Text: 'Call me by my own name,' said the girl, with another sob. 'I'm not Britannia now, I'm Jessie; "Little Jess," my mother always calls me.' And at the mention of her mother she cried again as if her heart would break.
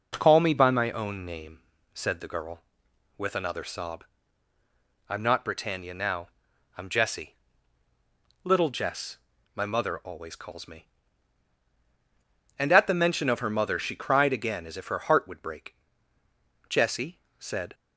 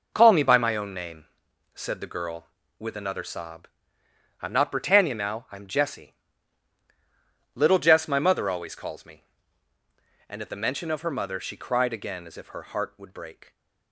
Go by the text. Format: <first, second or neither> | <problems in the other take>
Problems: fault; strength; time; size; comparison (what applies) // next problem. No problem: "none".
second | goes on to say "Jessie said"; noticeable; from 16.6 s on; 1.0 s long